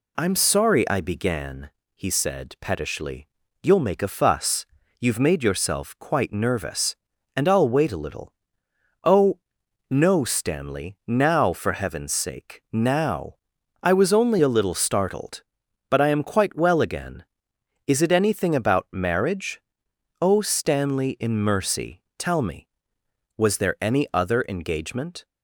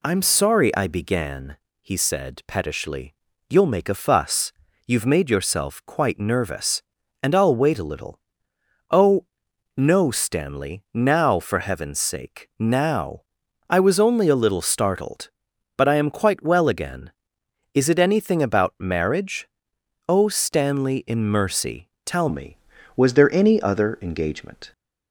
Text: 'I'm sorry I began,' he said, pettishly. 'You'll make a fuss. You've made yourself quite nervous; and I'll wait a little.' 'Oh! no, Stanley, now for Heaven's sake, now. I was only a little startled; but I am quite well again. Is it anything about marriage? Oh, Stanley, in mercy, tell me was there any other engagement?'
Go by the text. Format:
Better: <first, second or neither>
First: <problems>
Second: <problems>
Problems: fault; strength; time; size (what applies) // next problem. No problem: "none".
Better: first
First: none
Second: changes voice at "me"; from 22.2 s on; 2.5 s long